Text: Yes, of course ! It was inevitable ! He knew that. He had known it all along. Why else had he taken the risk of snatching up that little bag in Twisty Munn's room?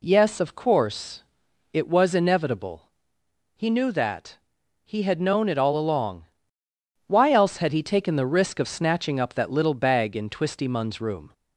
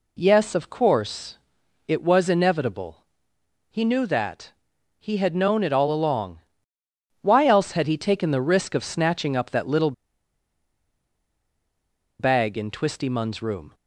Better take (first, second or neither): first